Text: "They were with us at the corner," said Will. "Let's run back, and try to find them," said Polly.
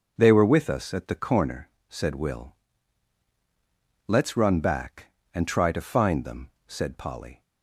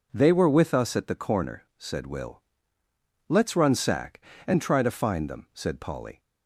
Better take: first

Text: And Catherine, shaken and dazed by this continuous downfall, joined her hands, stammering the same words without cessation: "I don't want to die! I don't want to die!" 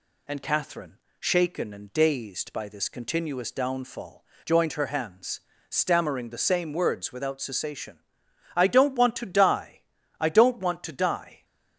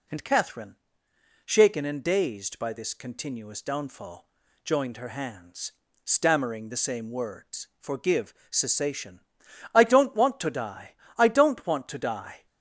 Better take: first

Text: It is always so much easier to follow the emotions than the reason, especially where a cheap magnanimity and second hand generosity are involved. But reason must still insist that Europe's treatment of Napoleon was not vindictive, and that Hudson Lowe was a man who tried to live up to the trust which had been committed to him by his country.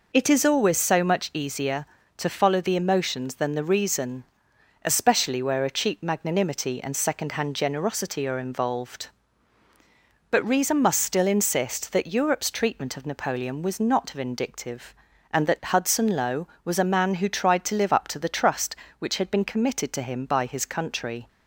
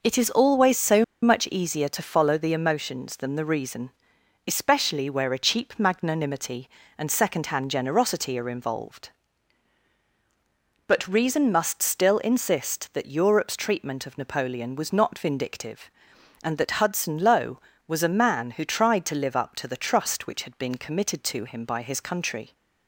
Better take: first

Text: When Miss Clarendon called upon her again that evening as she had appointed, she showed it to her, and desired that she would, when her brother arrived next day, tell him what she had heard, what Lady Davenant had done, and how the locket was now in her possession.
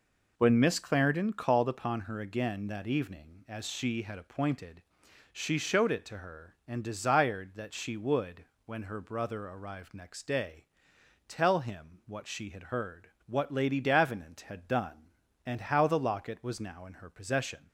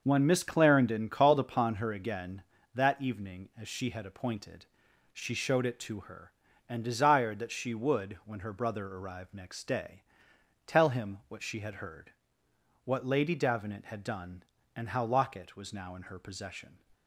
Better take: first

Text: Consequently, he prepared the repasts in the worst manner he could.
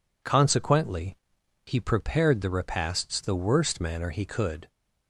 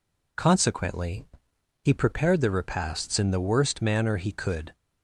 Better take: second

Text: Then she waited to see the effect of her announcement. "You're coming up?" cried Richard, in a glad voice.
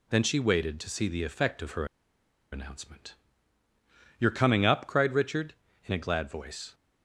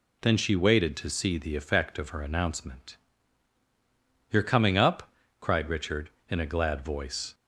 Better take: second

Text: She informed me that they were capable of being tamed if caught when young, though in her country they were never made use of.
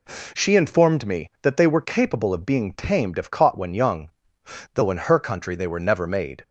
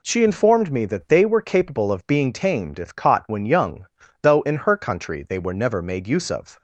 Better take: second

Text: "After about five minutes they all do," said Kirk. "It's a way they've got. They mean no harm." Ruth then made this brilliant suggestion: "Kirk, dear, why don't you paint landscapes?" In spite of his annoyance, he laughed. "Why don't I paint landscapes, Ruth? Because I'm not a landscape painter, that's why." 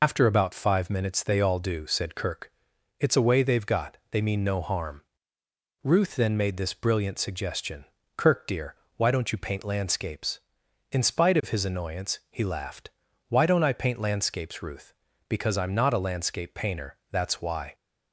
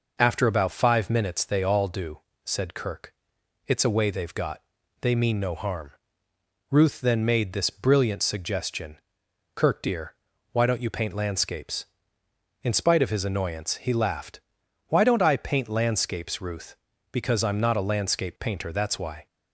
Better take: second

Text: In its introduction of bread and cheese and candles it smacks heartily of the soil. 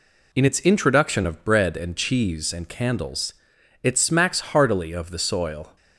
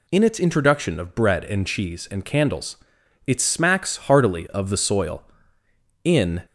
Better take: first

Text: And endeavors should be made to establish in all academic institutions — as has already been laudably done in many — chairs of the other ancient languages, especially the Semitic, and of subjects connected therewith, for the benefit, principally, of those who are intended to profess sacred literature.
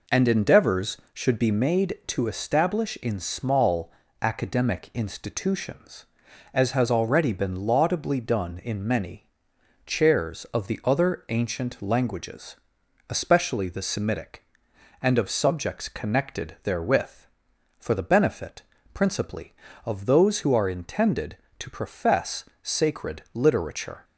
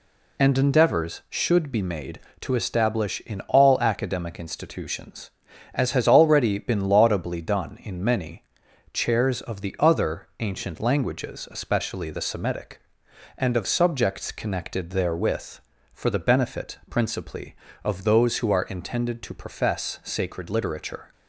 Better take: second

